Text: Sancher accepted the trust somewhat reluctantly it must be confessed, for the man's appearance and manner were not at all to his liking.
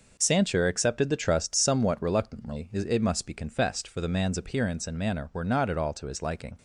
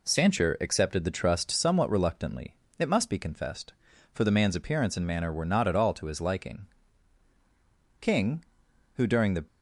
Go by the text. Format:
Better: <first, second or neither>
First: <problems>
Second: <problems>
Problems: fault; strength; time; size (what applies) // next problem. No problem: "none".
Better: first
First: none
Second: pauses between "reluctantly" and "it"; slight; at 2.5 s; 0.26 s long // goes on to say "King who during the"; from 8.0 s on; 1.4 s long